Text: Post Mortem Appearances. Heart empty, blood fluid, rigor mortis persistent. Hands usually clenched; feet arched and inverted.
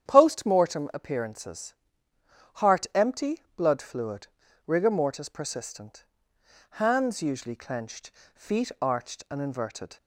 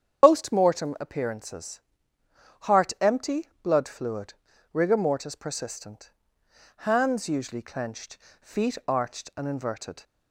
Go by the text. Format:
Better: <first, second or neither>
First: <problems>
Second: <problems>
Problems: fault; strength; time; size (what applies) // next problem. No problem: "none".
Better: first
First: starts louder than the rest; strong; until 1.1 s; 9 dB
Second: loses the start of "Post"; at 0.2 s; 100 ms // starts louder than the rest; strong; until 1.2 s; 8.5 dB